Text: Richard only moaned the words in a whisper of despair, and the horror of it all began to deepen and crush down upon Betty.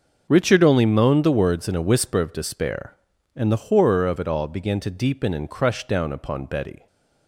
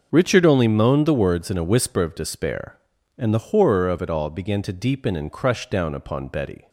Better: neither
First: starts louder than the rest; noticeable; until 1.3 s; 6 dB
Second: starts louder than the rest; noticeable; until 1.1 s; 6 dB

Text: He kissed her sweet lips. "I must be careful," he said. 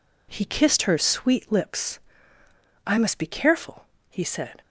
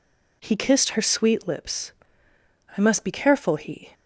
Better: first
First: none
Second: stops before "said"; at 3.9 s

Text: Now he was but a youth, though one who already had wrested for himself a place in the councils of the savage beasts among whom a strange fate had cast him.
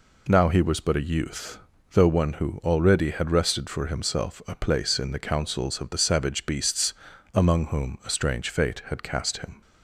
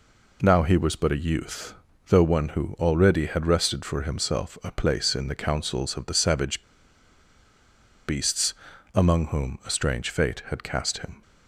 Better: first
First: pauses between "beasts" and "among"; at 6.9 s; 0.40 s long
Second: pauses between "savage" and "beasts"; strong; at 6.6 s; 1.4 s long // pauses between "beasts" and "among"; at 8.5 s; 0.40 s long

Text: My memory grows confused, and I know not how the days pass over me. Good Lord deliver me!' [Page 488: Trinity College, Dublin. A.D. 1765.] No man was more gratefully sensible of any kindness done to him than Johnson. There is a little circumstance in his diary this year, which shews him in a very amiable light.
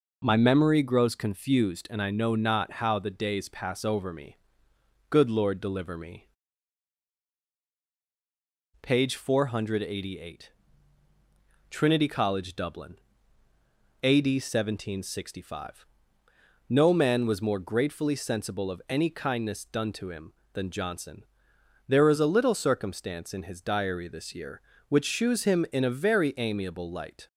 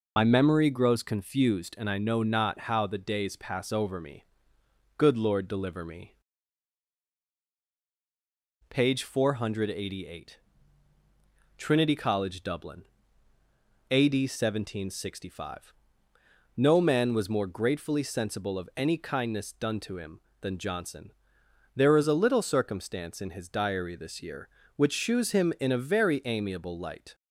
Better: first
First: none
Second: loses the start of "My"; at 0.1 s; 65 ms

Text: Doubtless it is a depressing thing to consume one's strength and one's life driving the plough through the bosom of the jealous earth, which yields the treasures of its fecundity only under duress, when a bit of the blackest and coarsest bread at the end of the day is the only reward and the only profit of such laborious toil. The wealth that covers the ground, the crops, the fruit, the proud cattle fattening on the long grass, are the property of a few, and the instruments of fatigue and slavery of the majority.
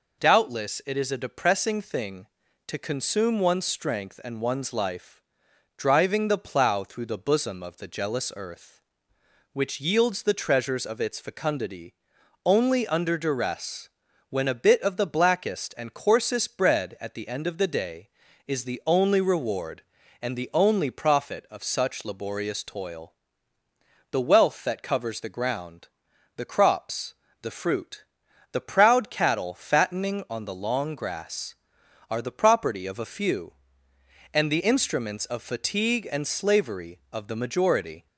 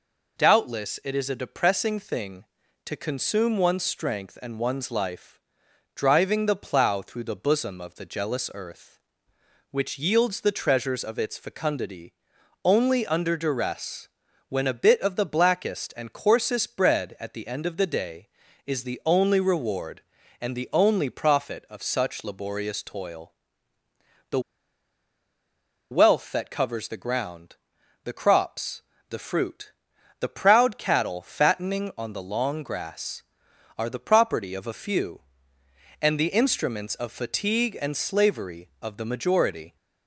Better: first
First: pauses between "life" and "driving"; noticeable; at 5.2 s; 0.56 s long // pauses between "fecundity" and "only"; noticeable; at 11.9 s; 0.50 s long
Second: pauses between "life" and "driving"; noticeable; at 5.3 s; 0.56 s long // pauses between "fecundity" and "only"; noticeable; at 12.1 s; 0.50 s long // pauses between "The" and "wealth"; strong; at 24.3 s; 1.5 s long

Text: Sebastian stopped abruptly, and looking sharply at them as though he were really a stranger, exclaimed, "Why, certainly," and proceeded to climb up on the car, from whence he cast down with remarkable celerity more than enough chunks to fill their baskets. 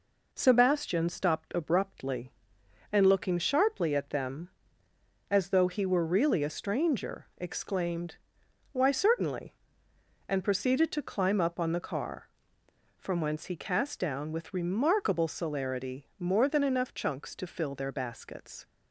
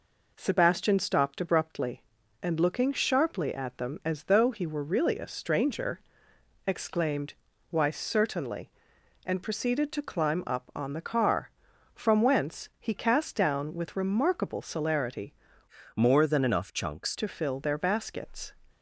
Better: first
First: none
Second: changes voice from "more" to "chunks"; from 15.9 to 17.1 s; 1.2 s long

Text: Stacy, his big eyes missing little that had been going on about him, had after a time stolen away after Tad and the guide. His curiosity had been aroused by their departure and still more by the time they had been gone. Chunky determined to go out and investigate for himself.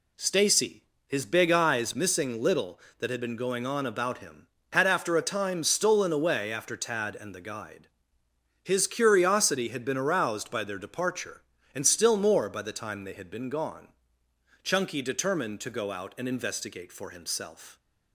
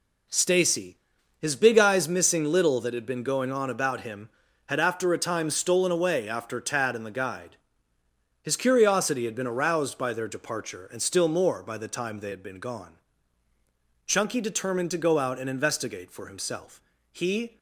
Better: first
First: none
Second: goes on to say "He"; slight; from 17.1 s on; 0.46 s long

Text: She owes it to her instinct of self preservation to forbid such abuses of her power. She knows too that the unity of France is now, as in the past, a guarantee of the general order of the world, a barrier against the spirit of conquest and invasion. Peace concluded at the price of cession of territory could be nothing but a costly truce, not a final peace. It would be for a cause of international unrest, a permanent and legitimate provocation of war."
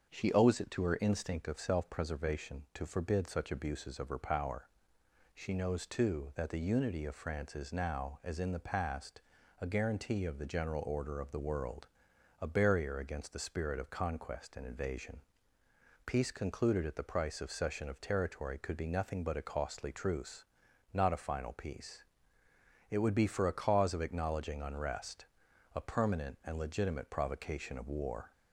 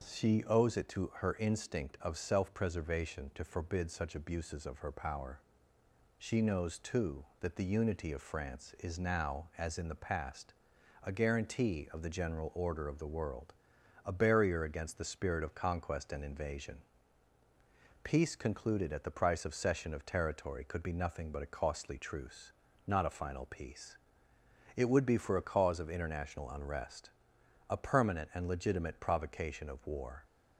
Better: second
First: starts louder than the rest; until 1.1 s; 6.5 dB // says "acknowledging" for "international"; at 24.0 s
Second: none

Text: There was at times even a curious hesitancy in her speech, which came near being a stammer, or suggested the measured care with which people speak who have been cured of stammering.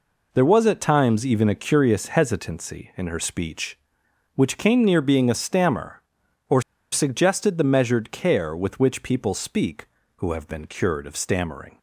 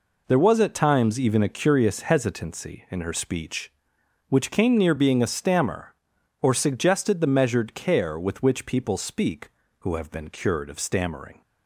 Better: second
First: pauses between "or" and "suggested"; slight; at 6.6 s; 0.31 s long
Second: none

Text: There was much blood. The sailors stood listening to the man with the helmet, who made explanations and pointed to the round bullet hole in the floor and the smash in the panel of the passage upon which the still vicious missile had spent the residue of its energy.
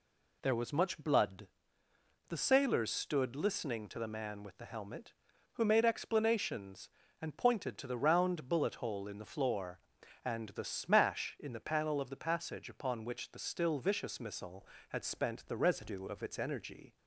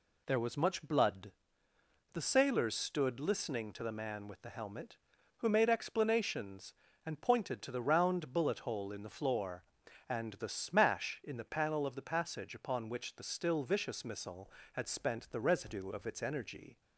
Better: neither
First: none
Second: none

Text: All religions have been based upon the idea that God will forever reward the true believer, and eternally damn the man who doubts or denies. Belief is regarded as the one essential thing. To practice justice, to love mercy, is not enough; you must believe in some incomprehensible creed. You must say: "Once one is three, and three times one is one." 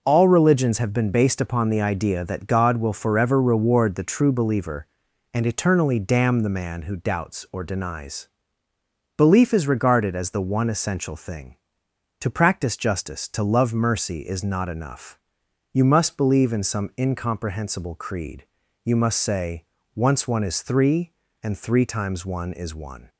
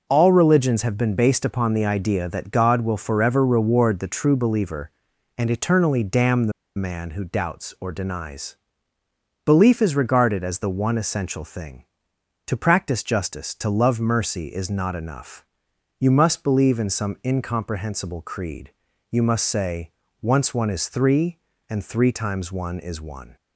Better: first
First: none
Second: pauses between "the" and "man"; slight; at 6.5 s; 0.25 s long

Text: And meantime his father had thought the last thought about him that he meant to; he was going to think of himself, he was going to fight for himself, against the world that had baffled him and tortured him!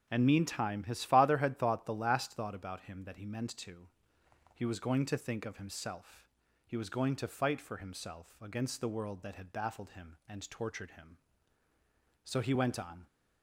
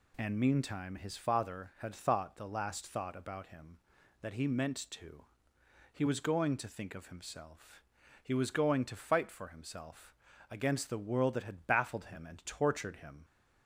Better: second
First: goes on to say "So he went on"; noticeable; from 12.2 s on; 0.83 s long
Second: none

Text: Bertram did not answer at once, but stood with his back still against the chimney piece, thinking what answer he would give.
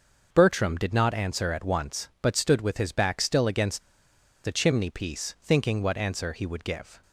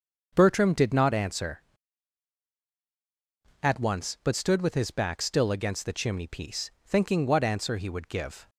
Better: second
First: starts louder than the rest; until 1.3 s; 6.5 dB // pauses between "against" and "the"; noticeable; at 3.8 s; 0.62 s long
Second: starts louder than the rest; until 1.3 s; 6.5 dB

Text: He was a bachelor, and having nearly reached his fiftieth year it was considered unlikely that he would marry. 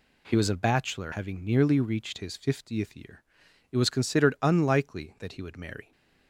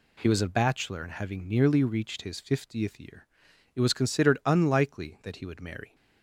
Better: second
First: skips "and"; at 1.1 s // pauses between "year" and "it"; noticeable; at 3.2 s; 0.48 s long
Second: pauses between "year" and "it"; noticeable; at 3.2 s; 0.48 s long

